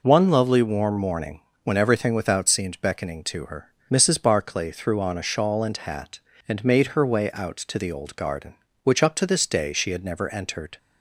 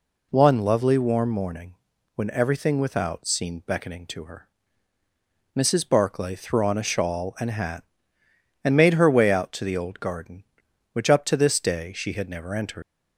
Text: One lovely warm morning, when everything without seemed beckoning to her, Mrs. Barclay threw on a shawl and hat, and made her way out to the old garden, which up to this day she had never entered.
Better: first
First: none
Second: leaves "entered" unfinished; at 12.8 s; 100 ms

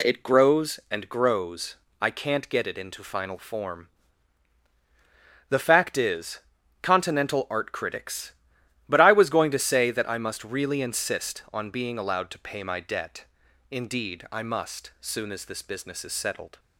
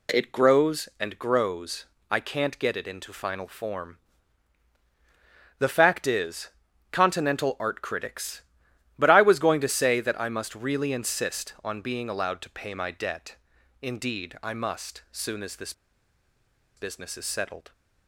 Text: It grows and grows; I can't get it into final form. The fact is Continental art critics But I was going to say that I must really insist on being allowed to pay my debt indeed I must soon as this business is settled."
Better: first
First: pauses between "is" and "Continental"; at 6.3 s; 0.42 s long // pauses between "debt" and "indeed"; noticeable; at 13.2 s; 0.46 s long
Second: pauses between "is" and "Continental"; at 6.4 s; 0.42 s long // pauses between "debt" and "indeed"; noticeable; at 13.3 s; 0.46 s long // pauses between "this" and "business"; at 15.7 s; 1.0 s long

